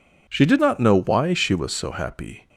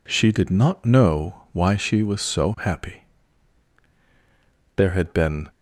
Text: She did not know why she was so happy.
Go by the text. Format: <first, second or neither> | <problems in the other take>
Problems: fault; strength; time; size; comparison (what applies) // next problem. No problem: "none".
first | goes on to say "There had been"; noticeable; from 4.7 s on; 0.72 s long